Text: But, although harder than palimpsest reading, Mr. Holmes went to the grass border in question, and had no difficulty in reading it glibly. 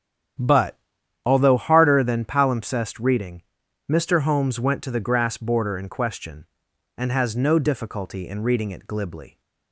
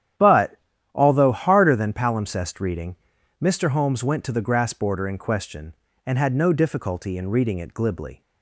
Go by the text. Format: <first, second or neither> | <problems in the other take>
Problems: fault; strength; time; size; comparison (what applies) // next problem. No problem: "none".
second | starts louder than the rest; strong; until 1.8 s; 9.5 dB; strong in the second // says "has" for "had"; at 7.0 s